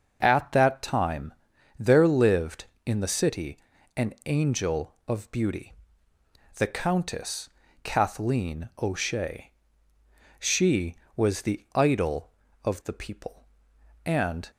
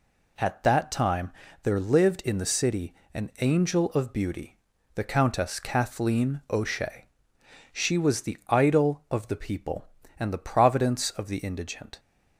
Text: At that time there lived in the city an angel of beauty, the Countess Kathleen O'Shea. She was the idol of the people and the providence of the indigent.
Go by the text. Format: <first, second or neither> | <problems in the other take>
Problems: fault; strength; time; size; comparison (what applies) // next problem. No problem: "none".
second | starts louder than the rest; until 1.2 s; 6 dB // pauses between "time" and "there"; noticeable; at 1.3 s; 0.46 s long; slight in the second // pauses between "city" and "an"; at 3.5 s; 0.40 s long; slight in the second // pauses between "Countess" and "Kathleen"; slight; at 7.4 s; 0.32 s long // stops before "the providence of the indigent"; at 14.5 s